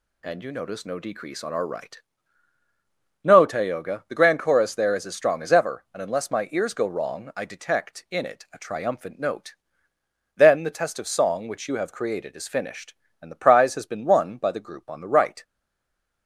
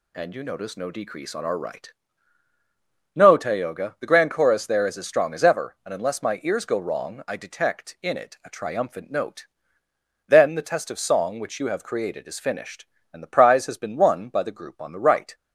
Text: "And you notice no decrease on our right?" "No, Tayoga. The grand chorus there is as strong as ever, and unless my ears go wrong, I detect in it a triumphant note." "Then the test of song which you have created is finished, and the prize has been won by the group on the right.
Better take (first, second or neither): second